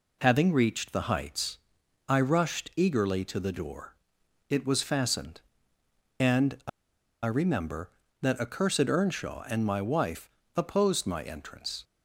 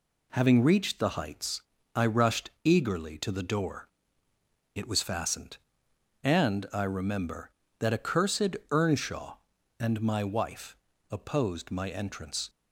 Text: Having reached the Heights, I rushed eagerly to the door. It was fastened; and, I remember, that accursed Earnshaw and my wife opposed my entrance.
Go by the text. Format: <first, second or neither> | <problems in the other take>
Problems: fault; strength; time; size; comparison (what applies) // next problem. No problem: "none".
second | pauses between "I" and "remember"; noticeable; at 6.6 s; 0.55 s long // pauses between "wife" and "opposed"; slight; at 10.2 s; 0.26 s long; slight in the second